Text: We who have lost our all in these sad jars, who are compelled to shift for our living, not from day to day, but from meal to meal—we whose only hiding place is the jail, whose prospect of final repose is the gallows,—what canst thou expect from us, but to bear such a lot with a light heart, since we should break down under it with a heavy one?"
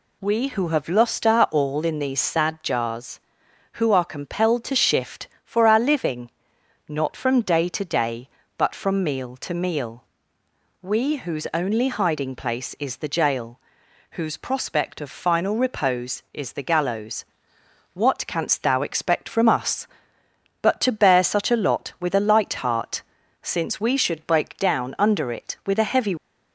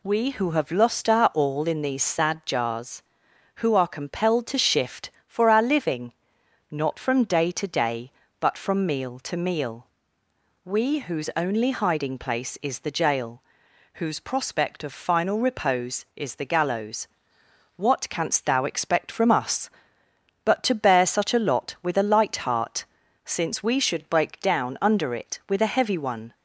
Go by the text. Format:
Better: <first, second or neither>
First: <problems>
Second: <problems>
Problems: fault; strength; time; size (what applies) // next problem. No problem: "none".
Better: second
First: stops before "one"; at 26.1 s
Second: none